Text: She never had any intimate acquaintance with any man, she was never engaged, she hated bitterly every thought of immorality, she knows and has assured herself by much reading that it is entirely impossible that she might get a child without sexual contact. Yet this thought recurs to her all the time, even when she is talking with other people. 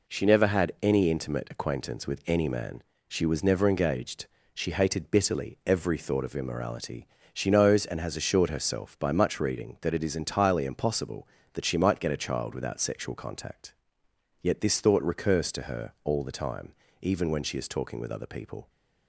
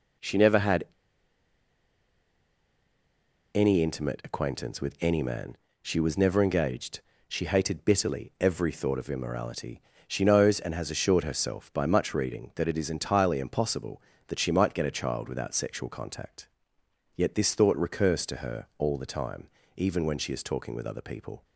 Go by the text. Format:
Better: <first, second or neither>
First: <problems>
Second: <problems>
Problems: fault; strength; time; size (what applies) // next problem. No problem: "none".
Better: first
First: none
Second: pauses between "had" and "any"; strong; at 0.8 s; 2.7 s long